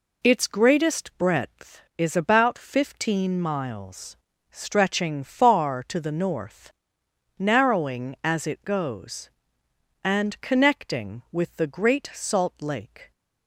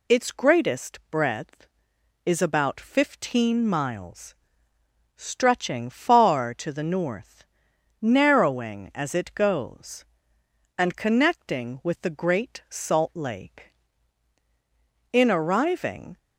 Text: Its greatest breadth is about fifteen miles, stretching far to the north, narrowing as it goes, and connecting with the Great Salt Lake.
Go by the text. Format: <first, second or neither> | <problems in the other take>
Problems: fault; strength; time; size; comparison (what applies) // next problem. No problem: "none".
first | goes on to say "In arriving"; noticeable; from 15.1 s on; 1.0 s long